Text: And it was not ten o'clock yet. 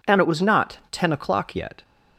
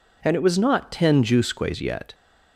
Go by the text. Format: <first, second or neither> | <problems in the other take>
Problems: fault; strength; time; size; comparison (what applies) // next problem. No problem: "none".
first | says "jusques" for "o'clock"; at 1.2 s